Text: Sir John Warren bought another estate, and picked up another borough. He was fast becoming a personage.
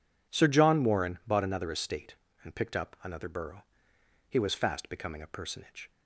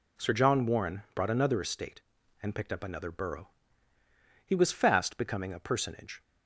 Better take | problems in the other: first | says "brought" for "bought"; at 1.1 s

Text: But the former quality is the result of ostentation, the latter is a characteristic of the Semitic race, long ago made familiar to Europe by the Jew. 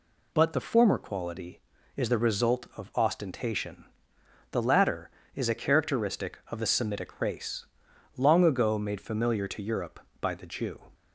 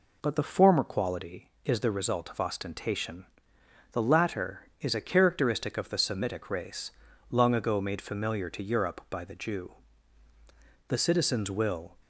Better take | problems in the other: first | goes on to say "The citizens will"; noticeable; from 10.8 s on; 1.1 s long

